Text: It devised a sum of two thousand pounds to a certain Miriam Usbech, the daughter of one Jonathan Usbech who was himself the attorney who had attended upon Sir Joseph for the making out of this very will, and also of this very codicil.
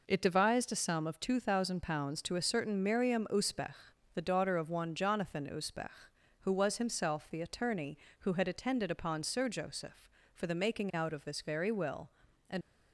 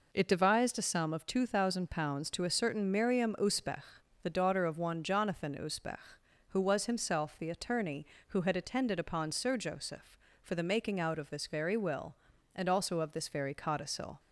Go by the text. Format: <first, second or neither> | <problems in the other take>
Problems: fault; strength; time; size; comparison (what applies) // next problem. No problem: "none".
second | stops before "also of this very codicil"; at 12.6 s